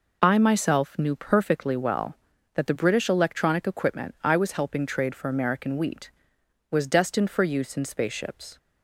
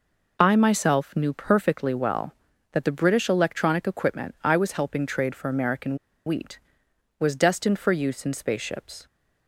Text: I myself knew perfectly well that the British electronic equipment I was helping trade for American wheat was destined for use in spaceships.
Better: first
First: none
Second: pauses between "American" and "wheat"; slight; at 5.9 s; 0.30 s long

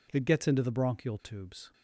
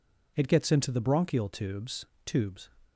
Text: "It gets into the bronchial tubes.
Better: first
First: none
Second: says "tubes" twice; at 2.2 s

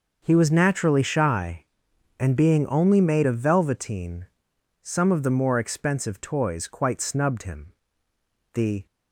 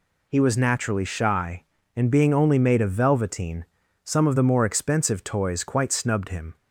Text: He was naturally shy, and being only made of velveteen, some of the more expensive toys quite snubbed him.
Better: second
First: starts louder than the rest; noticeable; until 1.2 s; 6 dB // goes on to say "The"; slight; from 8.5 s on; 0.32 s long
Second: none

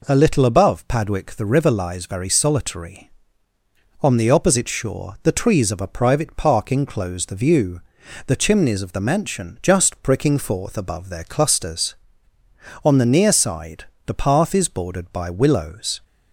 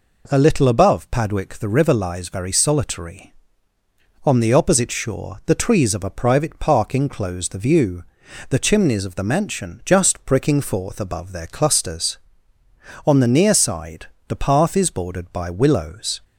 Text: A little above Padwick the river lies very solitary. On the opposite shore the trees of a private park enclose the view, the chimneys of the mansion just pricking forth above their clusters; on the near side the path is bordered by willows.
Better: neither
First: pauses between "side" and "the"; slight; at 13.8 s; 0.20 s long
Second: pauses between "side" and "the"; slight; at 14.0 s; 0.20 s long

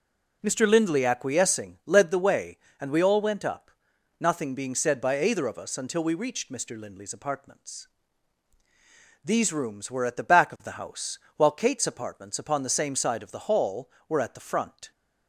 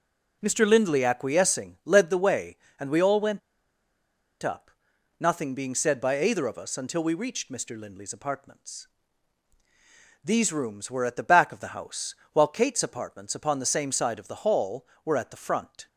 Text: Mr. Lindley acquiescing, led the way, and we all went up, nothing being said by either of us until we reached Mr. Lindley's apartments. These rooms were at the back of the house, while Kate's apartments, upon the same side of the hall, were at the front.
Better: first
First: none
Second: pauses between "went" and "up"; at 3.3 s; 1.0 s long

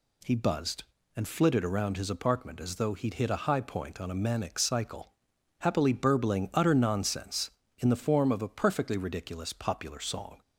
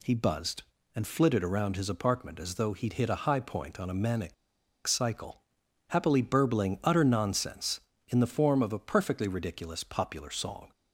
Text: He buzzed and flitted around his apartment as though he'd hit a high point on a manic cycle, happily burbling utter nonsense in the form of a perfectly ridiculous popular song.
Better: first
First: none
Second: pauses between "manic" and "cycle"; noticeable; at 4.3 s; 0.52 s long

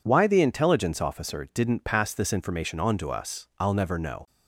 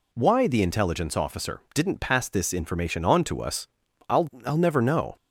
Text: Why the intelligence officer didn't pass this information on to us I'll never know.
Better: first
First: none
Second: pauses between "us" and "I'll"; at 3.6 s; 0.42 s long // says "I'll" twice; at 4.4 s

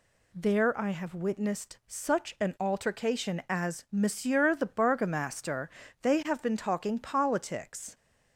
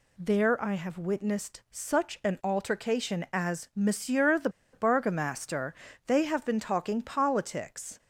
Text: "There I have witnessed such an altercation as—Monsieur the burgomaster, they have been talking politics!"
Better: first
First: none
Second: pauses between "the" and "burgomaster"; slight; at 4.4 s; 0.23 s long

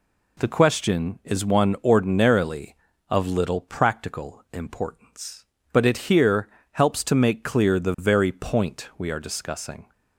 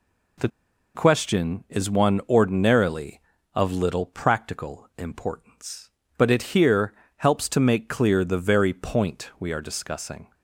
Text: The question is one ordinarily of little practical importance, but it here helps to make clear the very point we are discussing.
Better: first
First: pauses between "here" and "helps"; slight; at 6.4 s; 0.22 s long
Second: pauses between "The" and "question"; noticeable; at 0.4 s; 0.46 s long // pauses between "here" and "helps"; slight; at 6.9 s; 0.22 s long

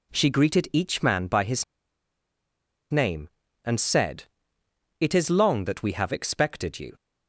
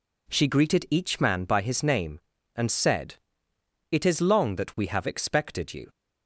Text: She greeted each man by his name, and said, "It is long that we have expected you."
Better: second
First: pauses between "his" and "name"; strong; at 1.6 s; 1.2 s long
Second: none

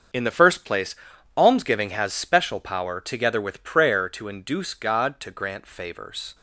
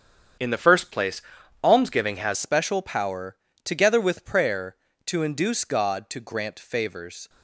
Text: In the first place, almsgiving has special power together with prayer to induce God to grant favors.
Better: first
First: starts louder than the rest; until 1.6 s; 7 dB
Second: starts louder than the rest; strong; until 1.8 s; 8 dB // changes voice at "special"; from 2.3 s on; 4.9 s long // pauses between "power" and "together"; slight; at 3.3 s; 0.26 s long

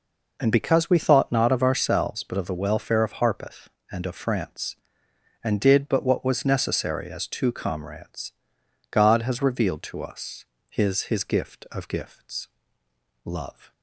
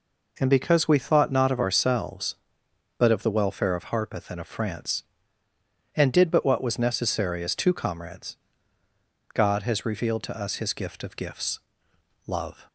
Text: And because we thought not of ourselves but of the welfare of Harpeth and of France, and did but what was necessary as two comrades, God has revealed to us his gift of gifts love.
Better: second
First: pauses between "us" and "his"; slight; at 10.4 s; 0.26 s long // says "his" twice; at 11.0 s // pauses between "gifts" and "love"; noticeable; at 12.4 s; 0.76 s long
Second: pauses between "gifts" and "love"; noticeable; at 11.5 s; 0.66 s long

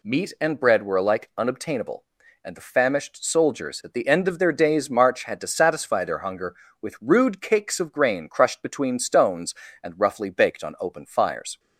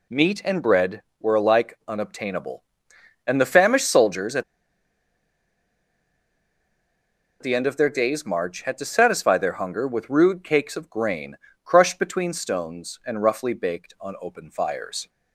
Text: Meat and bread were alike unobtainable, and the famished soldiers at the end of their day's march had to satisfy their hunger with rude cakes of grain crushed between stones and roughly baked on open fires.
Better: first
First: none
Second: pauses between "at" and "the"; strong; at 4.4 s; 2.9 s long // pauses between "grain" and "crushed"; slight; at 11.3 s; 0.30 s long

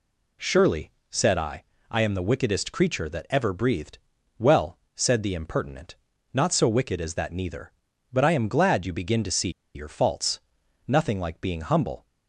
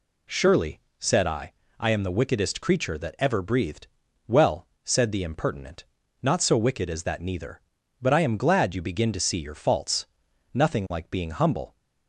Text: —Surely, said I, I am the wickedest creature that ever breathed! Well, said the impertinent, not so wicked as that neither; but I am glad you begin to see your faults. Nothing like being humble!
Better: second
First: pauses between "see" and "your"; slight; at 9.4 s; 0.25 s long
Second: none

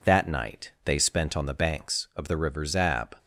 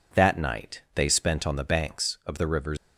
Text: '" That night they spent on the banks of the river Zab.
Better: first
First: none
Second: stops before "Zab"; at 2.7 s

